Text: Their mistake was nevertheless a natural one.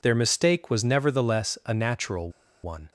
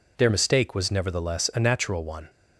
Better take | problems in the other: second | pauses between "natural" and "one"; slight; at 2.2 s; 0.34 s long

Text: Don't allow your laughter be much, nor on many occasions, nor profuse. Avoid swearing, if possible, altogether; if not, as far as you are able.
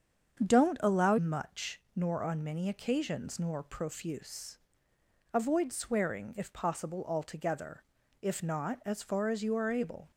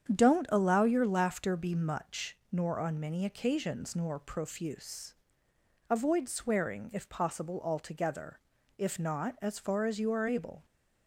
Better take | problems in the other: second | starts louder than the rest; strong; until 1.5 s; 7 dB; strong in the second // skips "your laughter be"; at 1.1 s

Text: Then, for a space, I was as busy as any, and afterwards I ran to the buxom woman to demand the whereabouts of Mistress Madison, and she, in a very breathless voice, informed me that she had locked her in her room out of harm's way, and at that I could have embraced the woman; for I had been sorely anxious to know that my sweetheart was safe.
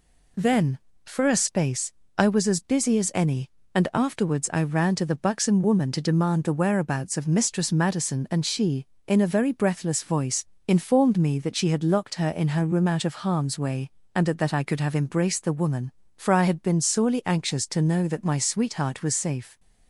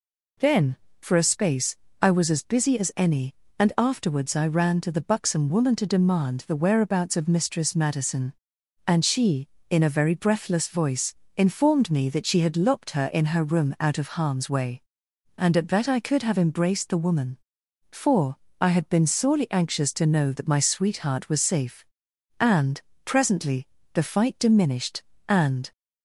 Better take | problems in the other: first | pauses between "for" and "I"; slight; at 18.3 s; 0.24 s long // goes on to say "And presently the fight diminished and"; strong; from 22.3 s on; 3.3 s long

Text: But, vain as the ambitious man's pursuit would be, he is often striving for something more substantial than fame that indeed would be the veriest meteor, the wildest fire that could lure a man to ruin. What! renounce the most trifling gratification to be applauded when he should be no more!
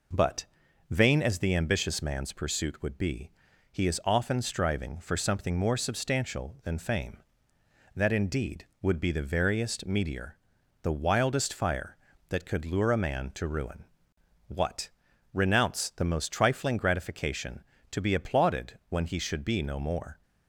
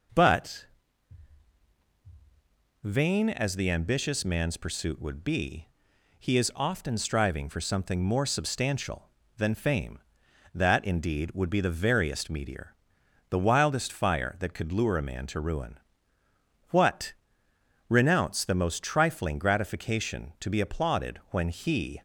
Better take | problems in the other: first | stops before "should be no more"; at 21.9 s

